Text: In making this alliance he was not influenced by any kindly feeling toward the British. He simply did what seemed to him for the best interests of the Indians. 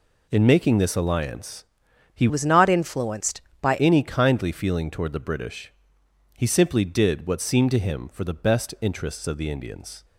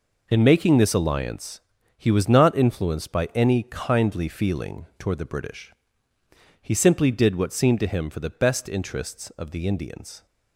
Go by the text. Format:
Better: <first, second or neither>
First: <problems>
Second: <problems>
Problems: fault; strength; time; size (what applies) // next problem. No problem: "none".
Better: second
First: pauses between "alliance" and "he"; noticeable; at 1.6 s; 0.50 s long // changes voice from "was" to "by"; from 2.2 to 3.7 s; 1.5 s long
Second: pauses between "alliance" and "he"; slight; at 1.6 s; 0.34 s long